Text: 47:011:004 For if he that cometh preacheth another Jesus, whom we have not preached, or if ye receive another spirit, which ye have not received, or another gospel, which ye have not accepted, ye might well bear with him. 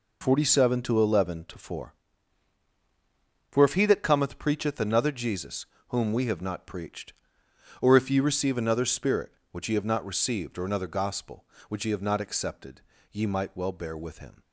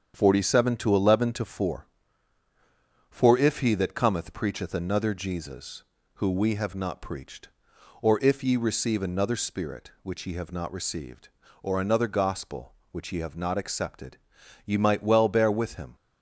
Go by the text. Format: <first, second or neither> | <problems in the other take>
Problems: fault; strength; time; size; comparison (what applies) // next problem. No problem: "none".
first | starts louder than the rest; strong; until 1.1 s; 8 dB // says "who" for "whom"; at 6.1 s